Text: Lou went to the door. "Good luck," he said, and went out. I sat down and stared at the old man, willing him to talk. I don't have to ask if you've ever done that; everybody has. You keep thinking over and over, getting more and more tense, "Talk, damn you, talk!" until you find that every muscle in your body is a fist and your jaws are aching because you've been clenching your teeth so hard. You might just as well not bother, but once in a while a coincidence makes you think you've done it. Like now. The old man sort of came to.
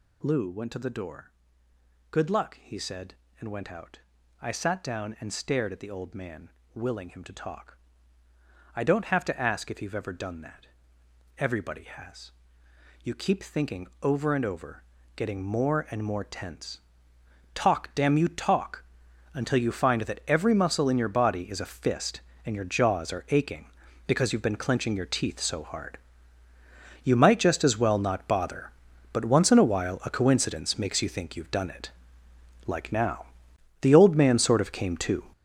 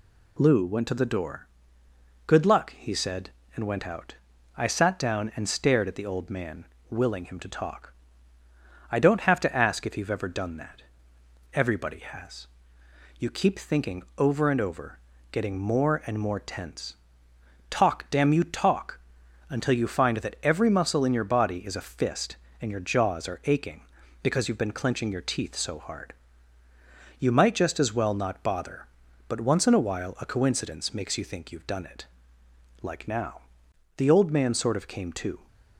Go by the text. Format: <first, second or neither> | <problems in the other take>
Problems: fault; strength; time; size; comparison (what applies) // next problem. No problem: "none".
second | gets louder; strong; throughout; 10 dB